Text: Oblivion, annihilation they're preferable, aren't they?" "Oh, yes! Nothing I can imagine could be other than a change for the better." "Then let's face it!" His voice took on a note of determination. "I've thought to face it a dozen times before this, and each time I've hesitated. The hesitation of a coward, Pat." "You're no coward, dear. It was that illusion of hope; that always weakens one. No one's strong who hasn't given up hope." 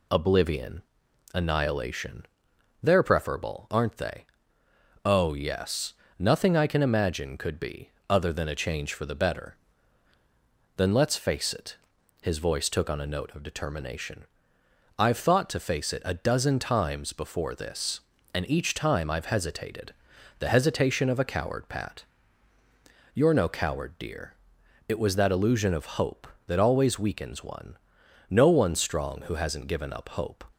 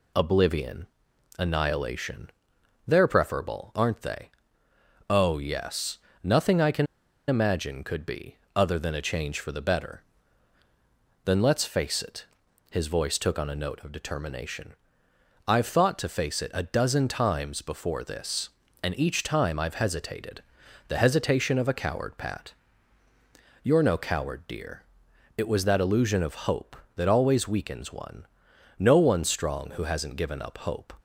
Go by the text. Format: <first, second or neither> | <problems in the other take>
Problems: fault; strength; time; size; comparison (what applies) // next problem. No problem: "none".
first | pauses between "annihilation" and "they're"; noticeable; at 2.2 s; 0.58 s long; noticeable in the first // pauses between "can" and "imagine"; at 6.8 s; 0.42 s long // pauses between "be" and "other"; slight; at 8.3 s; 0.20 s long; slight in the first